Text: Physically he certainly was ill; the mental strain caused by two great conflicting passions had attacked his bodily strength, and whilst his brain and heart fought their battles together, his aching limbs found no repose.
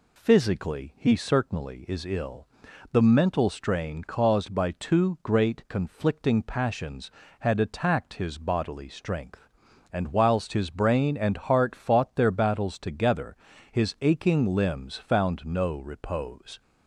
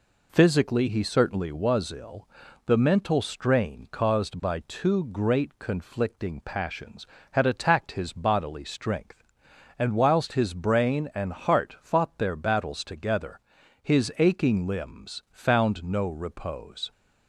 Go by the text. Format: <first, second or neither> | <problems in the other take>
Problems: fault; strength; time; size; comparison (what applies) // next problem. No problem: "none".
second | says "is" for "was"; at 1.8 s